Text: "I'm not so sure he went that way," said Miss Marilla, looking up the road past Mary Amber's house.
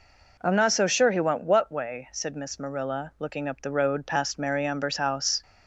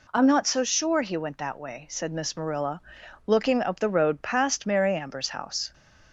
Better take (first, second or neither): second